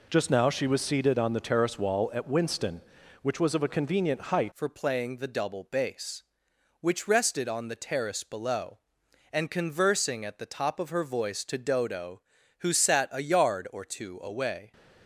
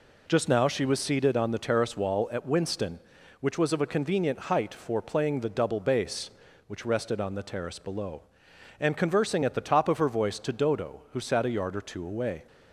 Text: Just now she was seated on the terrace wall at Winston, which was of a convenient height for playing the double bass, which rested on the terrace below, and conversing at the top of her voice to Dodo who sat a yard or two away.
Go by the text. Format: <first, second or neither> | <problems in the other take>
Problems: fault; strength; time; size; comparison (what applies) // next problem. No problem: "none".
second | changes voice at "for"; from 4.5 s on; 10.2 s long